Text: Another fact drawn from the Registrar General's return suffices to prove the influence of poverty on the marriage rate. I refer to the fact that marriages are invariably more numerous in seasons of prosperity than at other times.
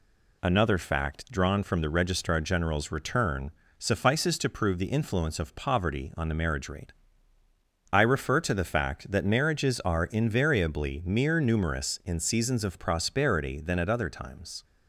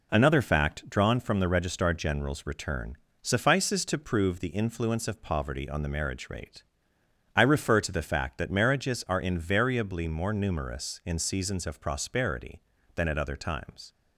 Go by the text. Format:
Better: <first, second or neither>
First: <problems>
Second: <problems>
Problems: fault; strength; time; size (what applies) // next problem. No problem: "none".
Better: second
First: pauses between "return" and "suffices"; slight; at 3.5 s; 0.26 s long // says "mere" for "more"; at 11.0 s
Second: pauses between "return" and "suffices"; slight; at 2.9 s; 0.26 s long